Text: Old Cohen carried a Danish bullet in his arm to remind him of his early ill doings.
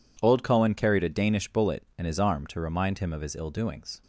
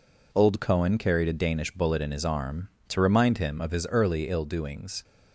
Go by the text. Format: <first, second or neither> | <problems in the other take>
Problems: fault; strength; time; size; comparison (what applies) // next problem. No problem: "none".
second | skips "early"; at 3.3 s